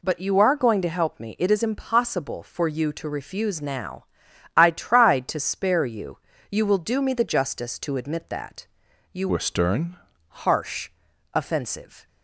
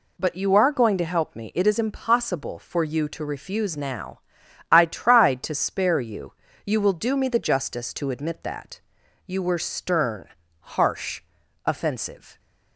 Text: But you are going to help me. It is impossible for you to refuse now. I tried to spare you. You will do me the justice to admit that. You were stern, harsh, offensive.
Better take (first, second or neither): second